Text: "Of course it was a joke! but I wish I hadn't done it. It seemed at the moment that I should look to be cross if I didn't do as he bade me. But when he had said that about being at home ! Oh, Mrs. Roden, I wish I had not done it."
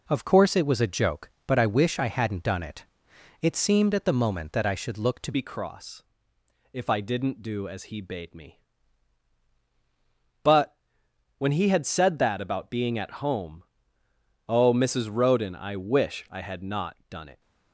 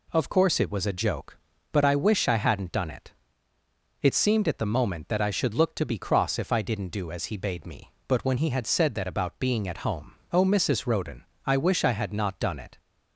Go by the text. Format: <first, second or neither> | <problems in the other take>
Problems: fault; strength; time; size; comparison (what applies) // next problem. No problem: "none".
second | changes voice at "be"; from 5.3 s on; 12.1 s long // pauses between "cross" and "if"; noticeable; at 6.0 s; 0.68 s long // pauses between "But" and "when"; noticeable; at 10.7 s; 0.62 s long // pauses between "not" and "done"; slight; at 16.9 s; 0.16 s long